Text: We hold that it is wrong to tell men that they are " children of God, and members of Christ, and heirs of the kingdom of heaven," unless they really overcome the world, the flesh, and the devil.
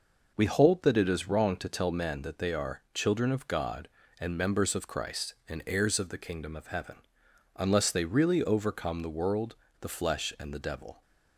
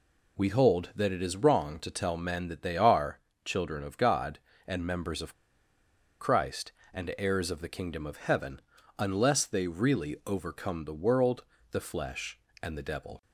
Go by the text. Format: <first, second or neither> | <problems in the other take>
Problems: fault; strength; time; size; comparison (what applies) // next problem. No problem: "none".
first | pauses between "of" and "Christ"; noticeable; at 5.3 s; 0.89 s long